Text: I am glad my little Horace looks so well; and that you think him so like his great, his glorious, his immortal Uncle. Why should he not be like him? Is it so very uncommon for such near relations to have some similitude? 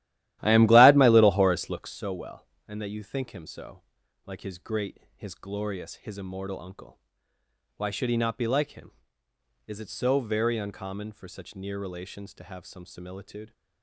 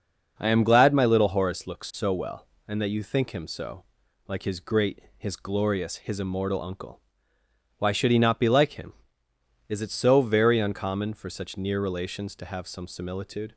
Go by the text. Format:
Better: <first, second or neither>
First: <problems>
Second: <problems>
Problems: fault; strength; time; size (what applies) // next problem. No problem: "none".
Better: second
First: starts louder than the rest; strong; until 1.9 s; 14 dB // pauses between "so" and "like"; noticeable; at 3.8 s; 0.46 s long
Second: pauses between "so" and "like"; noticeable; at 3.8 s; 0.46 s long